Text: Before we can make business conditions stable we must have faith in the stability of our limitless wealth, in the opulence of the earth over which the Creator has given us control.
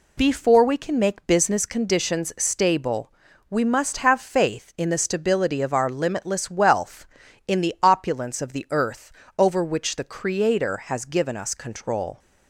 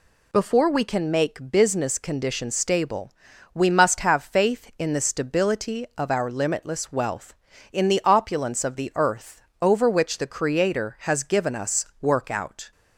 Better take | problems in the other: first | pauses between "stable" and "we"; at 3.1 s; 0.40 s long; slight in the first // pauses between "earth" and "over"; slight; at 9.4 s; 0.20 s long; slight in the first // says "workout" for "control"; at 12.0 s

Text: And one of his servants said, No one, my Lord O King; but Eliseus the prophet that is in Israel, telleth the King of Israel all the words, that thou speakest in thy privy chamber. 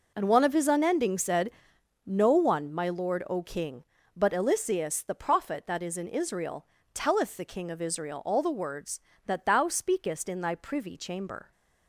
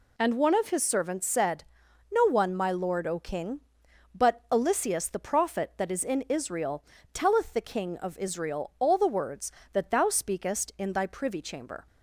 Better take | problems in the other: second | says "unending" for "servants"; at 0.6 s

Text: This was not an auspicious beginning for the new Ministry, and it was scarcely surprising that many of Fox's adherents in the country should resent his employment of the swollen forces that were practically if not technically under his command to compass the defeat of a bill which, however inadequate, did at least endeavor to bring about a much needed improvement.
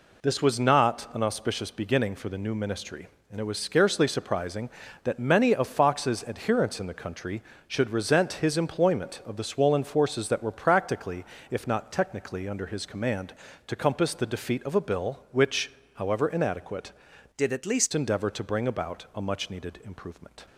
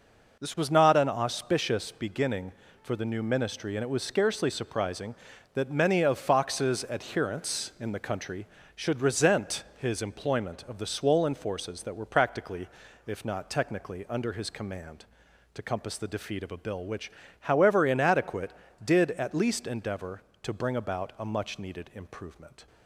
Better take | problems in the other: second | pauses between "practically" and "if"; slight; at 11.2 s; 0.28 s long; slight in the second // changes voice from "did" to "least"; from 17.3 to 17.9 s; 0.6 s long

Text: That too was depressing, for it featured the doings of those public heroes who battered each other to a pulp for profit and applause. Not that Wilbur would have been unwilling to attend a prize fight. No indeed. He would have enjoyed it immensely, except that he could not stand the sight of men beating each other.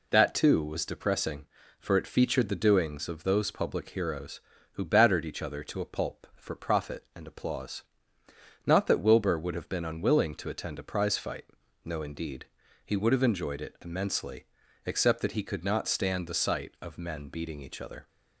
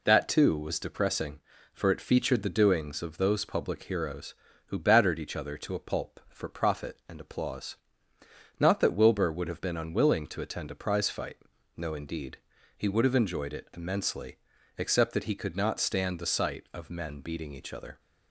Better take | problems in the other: neither | none

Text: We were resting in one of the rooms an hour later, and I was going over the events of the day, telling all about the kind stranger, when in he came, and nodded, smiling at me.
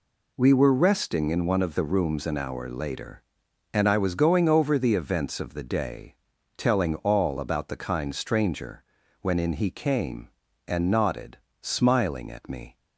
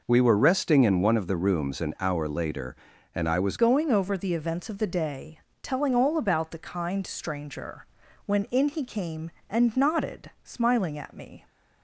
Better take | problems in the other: first | changes voice at "going"; from 3.5 s on; 7.9 s long

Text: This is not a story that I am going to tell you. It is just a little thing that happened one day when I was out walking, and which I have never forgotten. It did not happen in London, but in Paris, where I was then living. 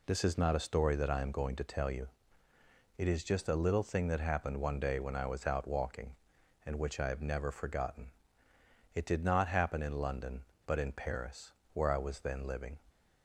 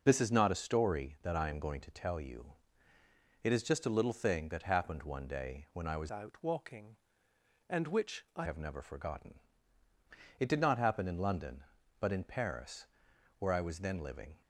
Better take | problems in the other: first | changes voice from "out" to "I"; from 6.1 to 8.4 s; 2.3 s long

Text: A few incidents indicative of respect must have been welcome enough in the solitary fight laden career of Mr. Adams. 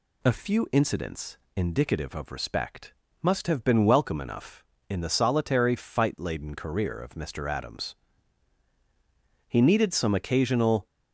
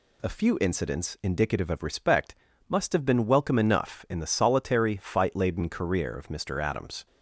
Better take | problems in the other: second | pauses between "incidents" and "indicative"; slight; at 1.3 s; 0.18 s long // pauses between "respect" and "must"; slight; at 2.9 s; 0.30 s long; slight in the second // goes on to say "He needed some occasional"; from 9.4 s on; 1.3 s long

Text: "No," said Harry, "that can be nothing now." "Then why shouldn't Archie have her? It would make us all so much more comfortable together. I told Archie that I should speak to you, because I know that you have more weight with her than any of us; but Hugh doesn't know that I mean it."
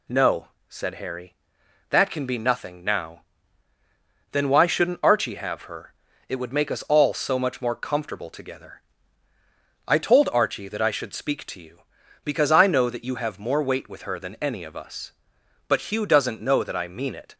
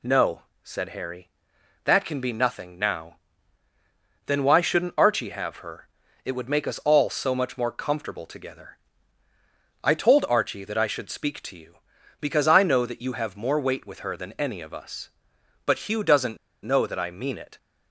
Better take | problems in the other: first | pauses between "doesn't" and "know"; slight; at 16.3 s; 0.28 s long

